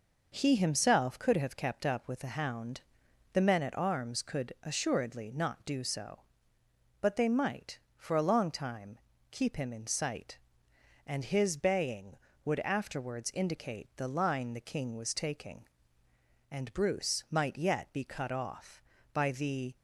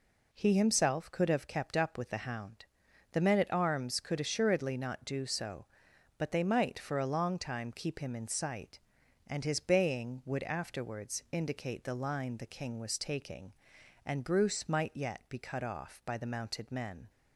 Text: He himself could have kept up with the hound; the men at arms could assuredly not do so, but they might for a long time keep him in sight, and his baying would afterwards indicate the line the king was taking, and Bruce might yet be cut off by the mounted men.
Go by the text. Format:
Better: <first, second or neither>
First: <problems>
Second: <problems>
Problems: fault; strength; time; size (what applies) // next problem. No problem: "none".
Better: second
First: pauses between "time" and "keep"; slight; at 8.9 s; 0.32 s long // stops before "mounted men"; at 19.7 s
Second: none